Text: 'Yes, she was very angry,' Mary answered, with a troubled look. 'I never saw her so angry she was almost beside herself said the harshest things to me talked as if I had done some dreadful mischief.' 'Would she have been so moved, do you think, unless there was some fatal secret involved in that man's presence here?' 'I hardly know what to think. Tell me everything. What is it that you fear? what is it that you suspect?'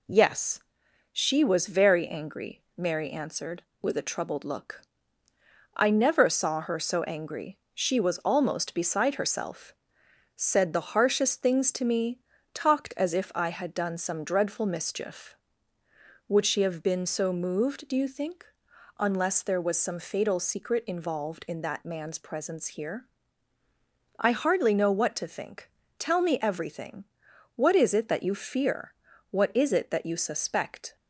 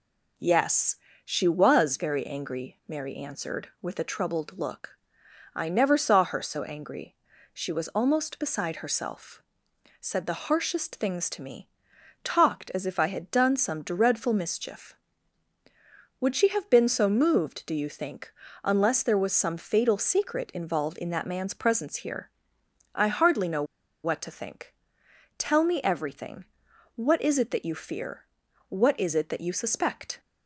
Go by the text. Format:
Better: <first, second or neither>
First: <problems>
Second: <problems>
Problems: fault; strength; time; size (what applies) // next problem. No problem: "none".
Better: first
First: pauses between "angry" and "she"; slight; at 7.5 s; 0.16 s long // pauses between "herself" and "said"; noticeable; at 9.7 s; 0.64 s long // pauses between "me" and "talked"; slight; at 12.2 s; 0.32 s long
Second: pauses between "angry" and "she"; at 7.1 s; 0.38 s long // pauses between "herself" and "said"; noticeable; at 9.4 s; 0.56 s long // pauses between "me" and "talked"; noticeable; at 11.6 s; 0.52 s long // pauses between "know" and "what"; at 23.6 s; 0.40 s long